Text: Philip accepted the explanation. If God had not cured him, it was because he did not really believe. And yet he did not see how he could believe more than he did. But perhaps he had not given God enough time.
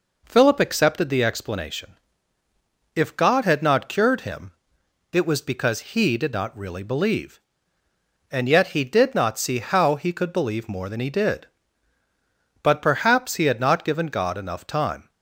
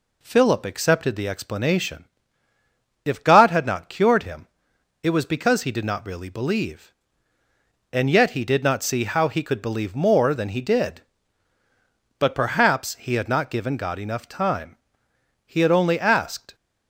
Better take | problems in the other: first | goes on to say "He had only asked"; noticeable; from 15.4 s on; 1.0 s long

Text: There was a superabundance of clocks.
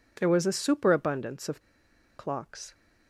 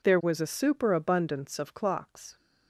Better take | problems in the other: second | pauses between "of" and "clocks"; noticeable; at 1.6 s; 0.55 s long

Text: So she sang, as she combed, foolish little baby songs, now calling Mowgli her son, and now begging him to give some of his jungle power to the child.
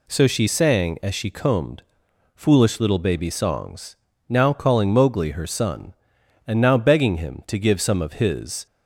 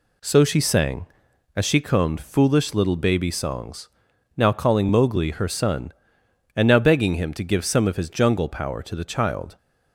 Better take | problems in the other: second | stops before "jungle power to the child"; at 8.6 s

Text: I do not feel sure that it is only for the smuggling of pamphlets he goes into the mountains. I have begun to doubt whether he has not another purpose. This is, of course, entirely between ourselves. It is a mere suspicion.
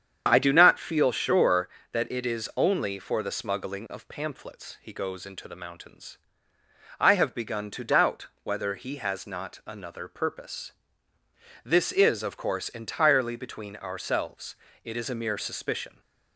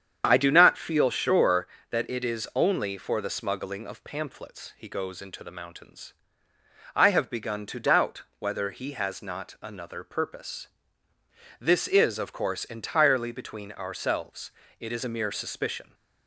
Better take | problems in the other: neither | starts louder than the rest; strong; the same in both // pauses between "doubt" and "whether"; slight; the same in both

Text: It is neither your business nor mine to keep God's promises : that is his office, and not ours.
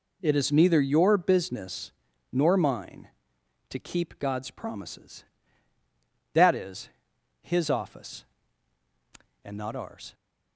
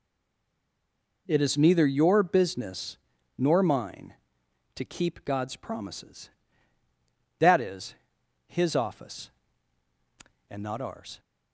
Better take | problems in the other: first | stays silent before the first word; noticeable; until 1.2 s; 1.2 s long // pauses between "business" and "nor"; at 2.9 s; 0.40 s long; also in the first // pauses between "is" and "his"; noticeable; at 7.9 s; 0.52 s long; noticeable in the first

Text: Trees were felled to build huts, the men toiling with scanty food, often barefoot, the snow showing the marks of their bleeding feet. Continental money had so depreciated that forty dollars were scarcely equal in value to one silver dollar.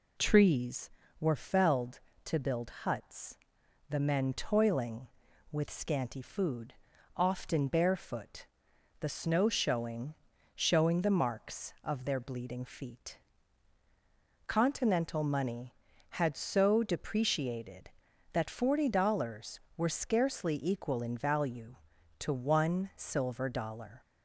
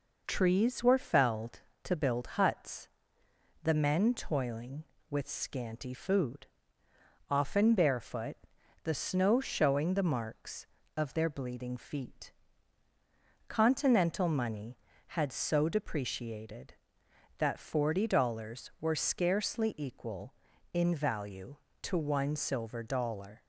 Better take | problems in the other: second | says "showing" twice; at 10.5 s

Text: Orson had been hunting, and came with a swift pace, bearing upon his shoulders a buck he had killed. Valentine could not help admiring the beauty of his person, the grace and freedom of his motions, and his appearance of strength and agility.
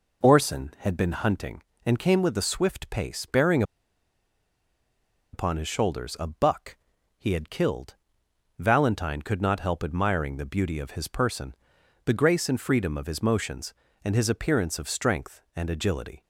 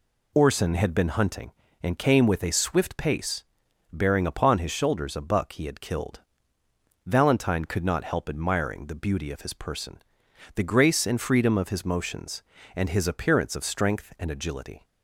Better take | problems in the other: second | pauses between "bearing" and "upon"; strong; at 3.6 s; 1.7 s long // pauses between "buck" and "he"; at 6.7 s; 0.42 s long

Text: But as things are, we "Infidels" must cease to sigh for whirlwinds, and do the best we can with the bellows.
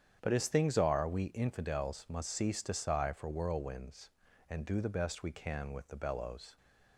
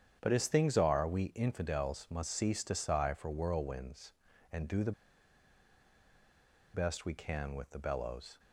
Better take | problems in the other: first | starts louder than the rest; strong; until 1.2 s; 8.5 dB; strong in the first // pauses between "the" and "best"; strong; at 4.9 s; 1.8 s long

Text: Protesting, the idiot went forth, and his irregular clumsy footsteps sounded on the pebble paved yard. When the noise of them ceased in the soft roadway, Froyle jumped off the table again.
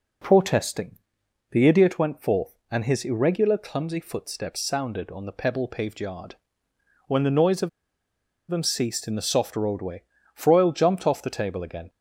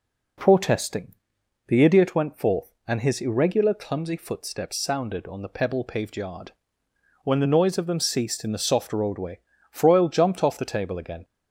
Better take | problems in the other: second | pauses between "of" and "them"; noticeable; at 7.6 s; 0.81 s long

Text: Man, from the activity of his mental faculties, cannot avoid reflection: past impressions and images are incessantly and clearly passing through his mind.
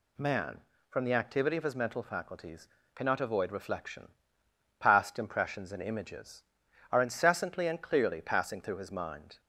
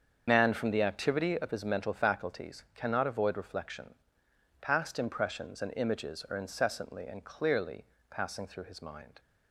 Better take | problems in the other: first | loses the start of "Man"; at 0.2 s; 55 ms // starts louder than the rest; strong; until 1.2 s; 7 dB // pauses between "clearly" and "passing"; slight; at 7.8 s; 0.26 s long

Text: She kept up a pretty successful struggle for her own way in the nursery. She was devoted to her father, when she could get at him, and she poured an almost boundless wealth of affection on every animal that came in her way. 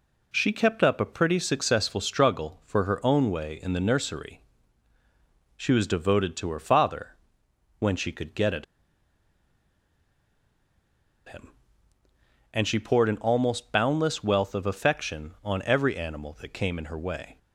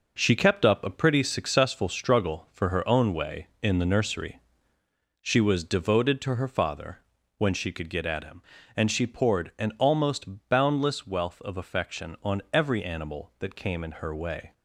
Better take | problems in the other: second | pauses between "at" and "him"; strong; at 8.6 s; 2.6 s long

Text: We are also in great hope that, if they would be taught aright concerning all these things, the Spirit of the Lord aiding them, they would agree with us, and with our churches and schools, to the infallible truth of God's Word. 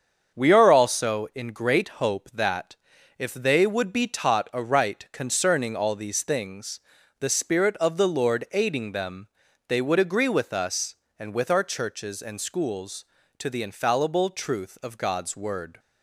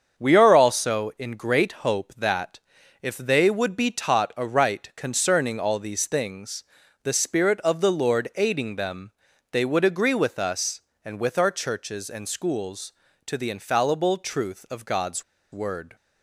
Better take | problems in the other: first | starts louder than the rest; until 1.2 s; 7 dB; also in the first // pauses between "God's" and "Word"; slight; at 15.2 s; 0.29 s long

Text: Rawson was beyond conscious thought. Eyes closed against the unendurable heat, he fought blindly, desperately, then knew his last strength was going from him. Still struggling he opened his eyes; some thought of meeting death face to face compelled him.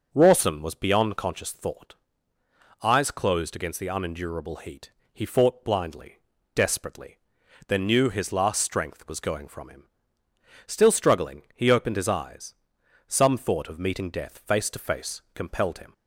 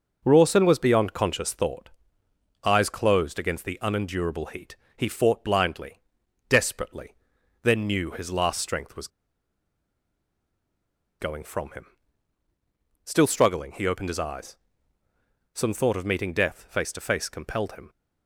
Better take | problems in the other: first | pauses between "was" and "going"; strong; at 9.0 s; 2.1 s long

